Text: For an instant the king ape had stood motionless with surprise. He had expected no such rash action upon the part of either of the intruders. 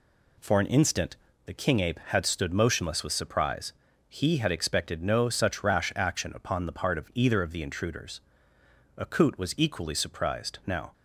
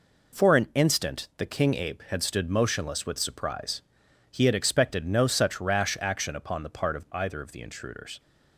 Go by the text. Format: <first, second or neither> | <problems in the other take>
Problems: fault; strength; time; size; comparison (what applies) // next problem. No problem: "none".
second | pauses between "instant" and "the"; slight; at 1.1 s; 0.28 s long // goes on to say "Akut was equally surprised Now"; strong; from 8.9 s on; 1.9 s long